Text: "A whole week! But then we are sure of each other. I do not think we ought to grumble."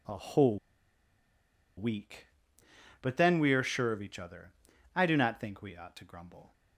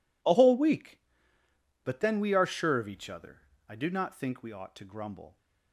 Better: second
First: pauses between "whole" and "week"; at 0.5 s; 1.2 s long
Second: none

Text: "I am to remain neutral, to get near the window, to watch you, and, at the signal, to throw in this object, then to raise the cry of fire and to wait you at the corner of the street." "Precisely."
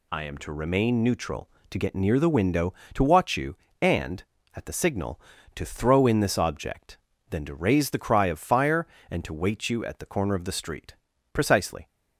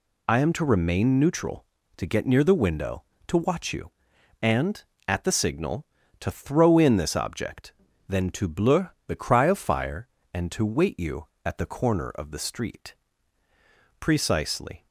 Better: first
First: none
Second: says "bleu" for "raise"; at 8.4 s

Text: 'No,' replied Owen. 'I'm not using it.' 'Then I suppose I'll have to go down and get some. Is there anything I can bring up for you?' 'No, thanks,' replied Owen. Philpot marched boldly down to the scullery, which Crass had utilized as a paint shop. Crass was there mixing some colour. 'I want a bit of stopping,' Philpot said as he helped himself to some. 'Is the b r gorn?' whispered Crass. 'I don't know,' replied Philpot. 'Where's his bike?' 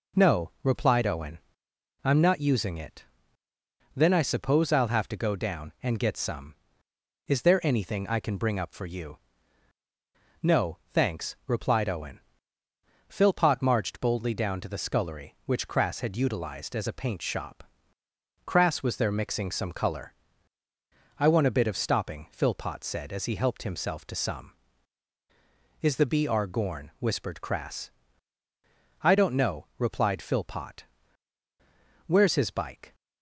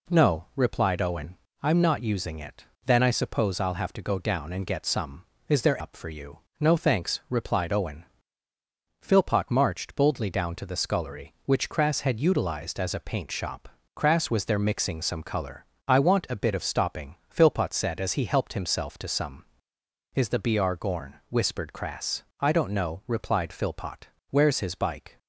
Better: first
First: none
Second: skips "anything I can bring"; at 5.8 s

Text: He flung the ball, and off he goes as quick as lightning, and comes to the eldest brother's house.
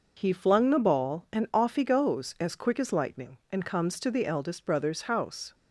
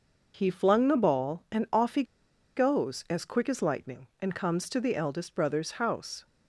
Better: first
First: none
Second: pauses between "he" and "goes"; noticeable; at 2.0 s; 0.53 s long

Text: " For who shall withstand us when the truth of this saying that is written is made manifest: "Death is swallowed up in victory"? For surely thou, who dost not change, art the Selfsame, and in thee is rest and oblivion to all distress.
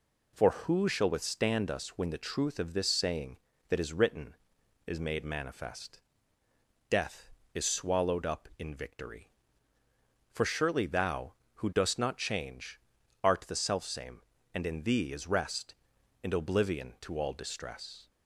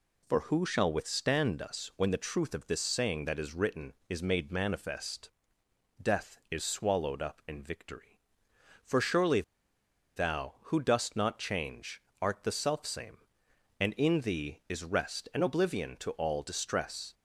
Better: first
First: none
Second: pauses between "surely" and "thou"; noticeable; at 9.4 s; 0.74 s long

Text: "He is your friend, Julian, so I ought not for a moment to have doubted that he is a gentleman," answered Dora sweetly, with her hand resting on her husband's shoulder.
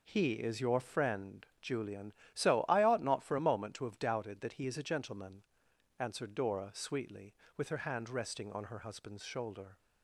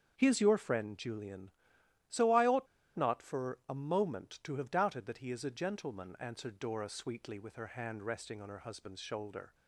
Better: first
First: none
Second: starts louder than the rest; strong; until 1.1 s; 7 dB // pauses between "ought" and "not"; slight; at 2.6 s; 0.31 s long

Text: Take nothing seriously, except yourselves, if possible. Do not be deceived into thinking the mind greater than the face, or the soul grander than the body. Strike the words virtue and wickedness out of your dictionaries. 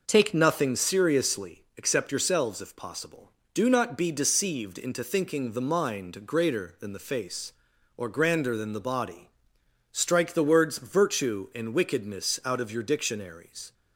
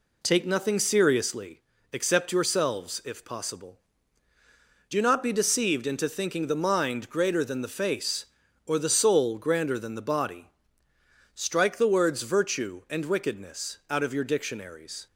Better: second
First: skips "the soul"; at 8.0 s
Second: none

